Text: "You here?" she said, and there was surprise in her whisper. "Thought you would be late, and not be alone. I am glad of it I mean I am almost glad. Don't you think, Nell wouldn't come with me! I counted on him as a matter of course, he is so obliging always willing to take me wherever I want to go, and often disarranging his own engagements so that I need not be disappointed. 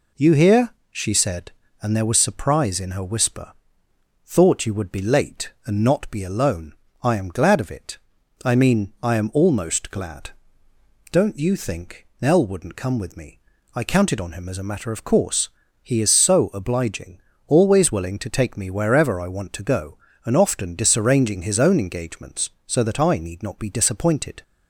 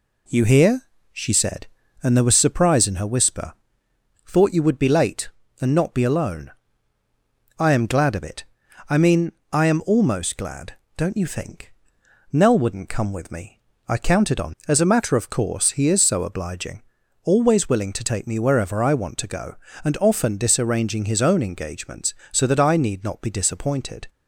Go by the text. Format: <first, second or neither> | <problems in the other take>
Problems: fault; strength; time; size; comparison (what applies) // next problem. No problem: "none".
first | pauses between "it" and "I"; noticeable; at 8.4 s; 0.46 s long; noticeable in the first // pauses between "mean" and "I"; slight; at 9.3 s; 0.20 s long // skips "him"; at 14.6 s // pauses between "obliging" and "always"; at 16.8 s; 0.42 s long; slight in the first